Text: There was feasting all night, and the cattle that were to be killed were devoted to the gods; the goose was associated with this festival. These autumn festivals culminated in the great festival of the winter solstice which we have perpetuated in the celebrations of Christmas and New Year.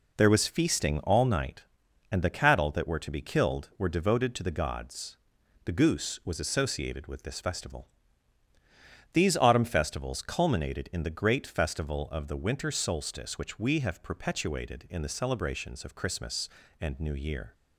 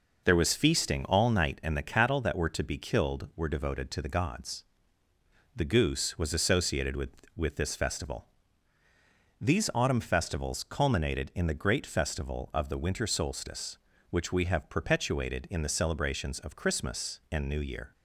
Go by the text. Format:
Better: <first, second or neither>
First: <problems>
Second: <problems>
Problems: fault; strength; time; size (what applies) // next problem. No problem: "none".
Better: first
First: none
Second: says "with" twice; at 7.3 s